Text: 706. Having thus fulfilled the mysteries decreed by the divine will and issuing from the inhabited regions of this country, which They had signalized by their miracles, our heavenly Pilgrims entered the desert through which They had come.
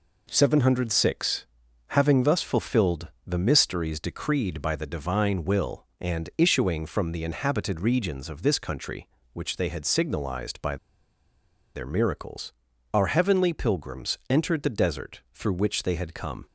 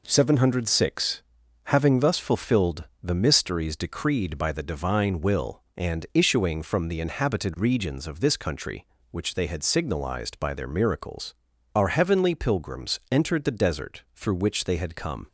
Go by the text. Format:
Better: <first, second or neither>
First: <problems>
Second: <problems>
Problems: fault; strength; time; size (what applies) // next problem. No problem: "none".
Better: second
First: pauses between "fulfilled" and "the"; slight; at 3.0 s; 0.18 s long // pauses between "by" and "their"; at 10.7 s; 0.98 s long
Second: pauses between "fulfilled" and "the"; slight; at 2.8 s; 0.18 s long